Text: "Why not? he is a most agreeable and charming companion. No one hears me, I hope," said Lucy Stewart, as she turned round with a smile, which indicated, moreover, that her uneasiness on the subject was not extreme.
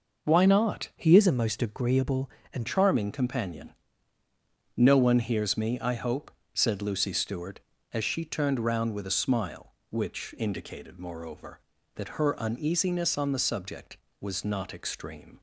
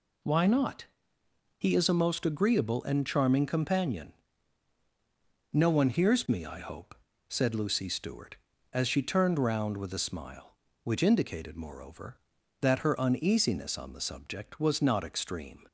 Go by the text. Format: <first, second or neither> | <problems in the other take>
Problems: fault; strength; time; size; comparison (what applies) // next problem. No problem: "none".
second | changes voice from "he" to "and"; from 0.9 to 2.6 s; 1.7 s long